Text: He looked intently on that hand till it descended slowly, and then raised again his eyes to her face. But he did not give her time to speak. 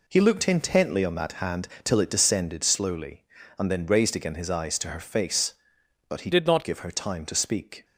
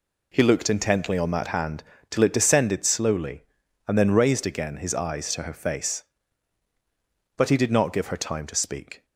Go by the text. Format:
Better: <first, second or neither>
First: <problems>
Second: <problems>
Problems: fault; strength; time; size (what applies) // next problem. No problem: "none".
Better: second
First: pauses between "hand" and "till"; slight; at 1.6 s; 0.16 s long // changes voice from "did" to "not"; from 6.3 to 6.6 s; 0.3 s long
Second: pauses between "hand" and "till"; slight; at 1.8 s; 0.26 s long